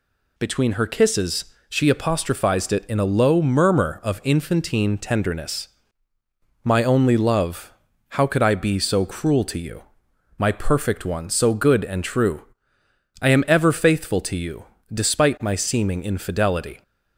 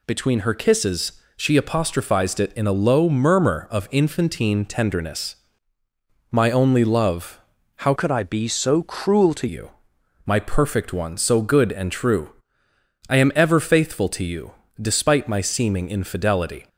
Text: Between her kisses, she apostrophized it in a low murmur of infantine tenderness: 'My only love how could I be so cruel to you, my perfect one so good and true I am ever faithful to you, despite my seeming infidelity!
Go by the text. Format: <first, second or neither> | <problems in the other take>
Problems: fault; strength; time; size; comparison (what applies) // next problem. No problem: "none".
first | pauses between "love" and "how"; at 7.3 s; 0.38 s long; also in the first // changes voice from "could" to "to"; from 7.9 to 9.4 s; 1.5 s long // pauses between "true" and "I"; noticeable; at 12.2 s; 0.80 s long; noticeable in the first